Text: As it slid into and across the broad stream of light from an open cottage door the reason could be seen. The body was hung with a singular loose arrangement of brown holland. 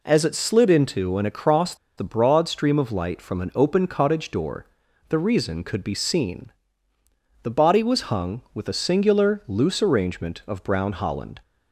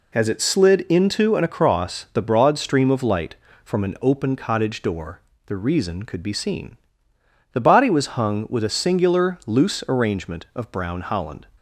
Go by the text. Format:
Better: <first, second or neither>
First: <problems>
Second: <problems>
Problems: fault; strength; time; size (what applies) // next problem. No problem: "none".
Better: second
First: pauses between "across" and "the"; slight; at 1.7 s; 0.22 s long // pauses between "door" and "the"; at 4.6 s; 0.42 s long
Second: pauses between "door" and "the"; slight; at 5.2 s; 0.26 s long